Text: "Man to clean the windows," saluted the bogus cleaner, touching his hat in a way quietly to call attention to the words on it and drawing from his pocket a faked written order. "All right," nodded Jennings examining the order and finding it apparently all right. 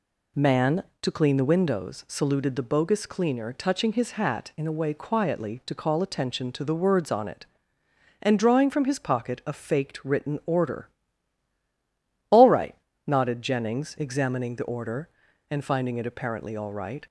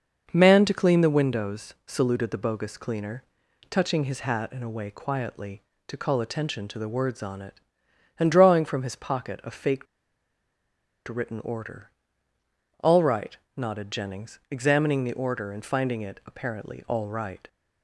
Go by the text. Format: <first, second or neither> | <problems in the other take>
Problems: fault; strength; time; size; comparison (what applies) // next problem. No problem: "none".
first | starts louder than the rest; until 1.3 s; 6 dB // pauses between "faked" and "written"; at 9.8 s; 1.2 s long